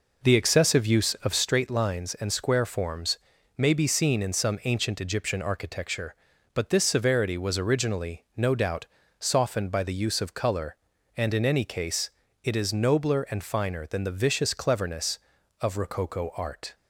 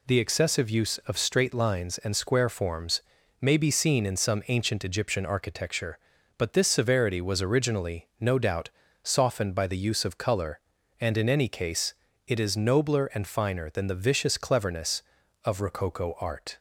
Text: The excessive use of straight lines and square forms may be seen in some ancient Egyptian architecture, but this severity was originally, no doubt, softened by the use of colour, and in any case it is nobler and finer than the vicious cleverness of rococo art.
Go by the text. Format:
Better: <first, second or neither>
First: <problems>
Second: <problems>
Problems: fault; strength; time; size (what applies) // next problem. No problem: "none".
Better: second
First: starts louder than the rest; noticeable; until 1.5 s; 4.5 dB // pauses between "forms" and "may"; at 3.1 s; 0.38 s long // pauses between "case" and "it"; slight; at 12.1 s; 0.32 s long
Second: pauses between "forms" and "may"; at 3.0 s; 0.38 s long // pauses between "case" and "it"; slight; at 11.9 s; 0.32 s long